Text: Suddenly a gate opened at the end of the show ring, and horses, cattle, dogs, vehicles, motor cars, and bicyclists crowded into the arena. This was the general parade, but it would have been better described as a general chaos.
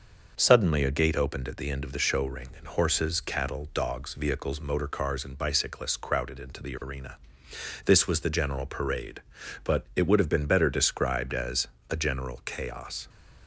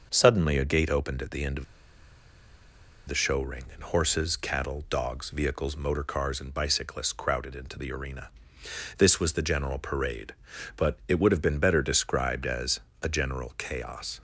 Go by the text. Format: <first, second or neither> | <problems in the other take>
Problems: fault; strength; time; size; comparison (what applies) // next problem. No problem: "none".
first | starts louder than the rest; until 1.1 s; 6.5 dB; also in the first // pauses between "of" and "the"; strong; at 1.6 s; 1.4 s long // pauses between "as" and "a"; slight; at 12.7 s; 0.22 s long; slight in the first